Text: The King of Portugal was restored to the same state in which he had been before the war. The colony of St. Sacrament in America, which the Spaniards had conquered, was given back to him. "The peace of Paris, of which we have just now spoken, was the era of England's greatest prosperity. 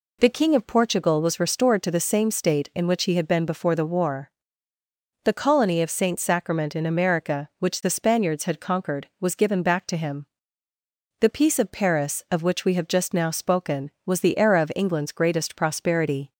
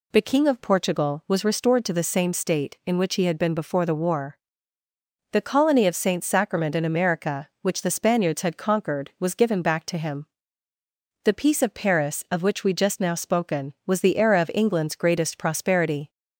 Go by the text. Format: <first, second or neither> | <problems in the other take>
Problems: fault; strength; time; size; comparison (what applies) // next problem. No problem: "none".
first | skips "have"; at 12.7 s